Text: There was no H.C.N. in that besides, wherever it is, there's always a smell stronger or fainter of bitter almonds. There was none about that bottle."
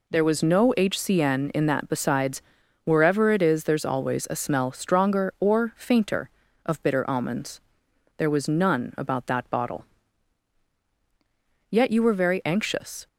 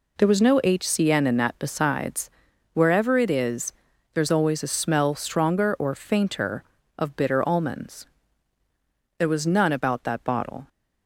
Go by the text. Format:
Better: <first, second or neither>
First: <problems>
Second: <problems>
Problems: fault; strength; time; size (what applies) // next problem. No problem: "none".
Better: second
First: goes on to say "Yet you were very anxious"; from 11.6 s on; 1.3 s long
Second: none